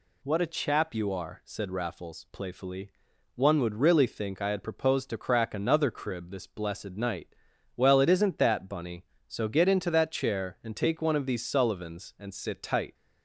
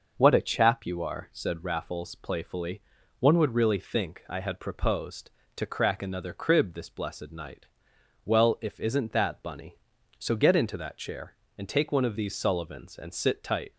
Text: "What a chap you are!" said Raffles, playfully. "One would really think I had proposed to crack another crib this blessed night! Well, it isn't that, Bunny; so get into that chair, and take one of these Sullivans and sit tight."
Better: first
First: none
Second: says "if" for "it"; at 8.6 s

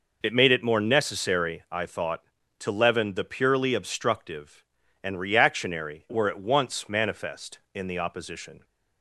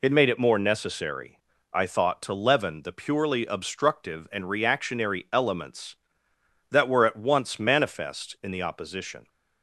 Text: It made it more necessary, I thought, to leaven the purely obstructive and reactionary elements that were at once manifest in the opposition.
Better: second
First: skips "elements that"; at 6.0 s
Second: none

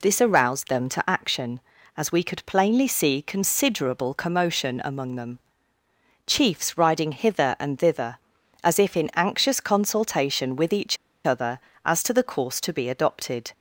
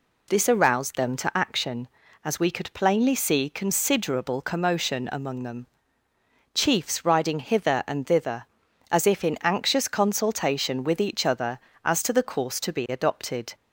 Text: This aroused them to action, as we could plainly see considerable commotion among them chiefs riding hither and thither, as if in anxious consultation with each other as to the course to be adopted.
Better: second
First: pauses between "them" and "chiefs"; noticeable; at 5.3 s; 0.88 s long // pauses between "each" and "other"; slight; at 10.9 s; 0.29 s long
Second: pauses between "them" and "chiefs"; noticeable; at 5.6 s; 0.88 s long

